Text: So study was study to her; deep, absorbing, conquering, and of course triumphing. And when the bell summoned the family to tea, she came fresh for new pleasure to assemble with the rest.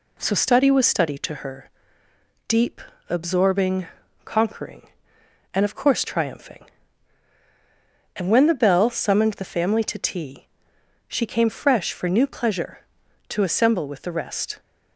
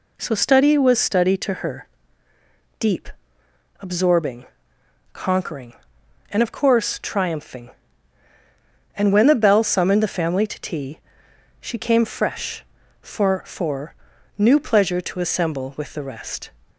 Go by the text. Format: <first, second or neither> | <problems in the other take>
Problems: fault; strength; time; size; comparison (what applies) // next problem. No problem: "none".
first | says "for" twice; at 13.4 s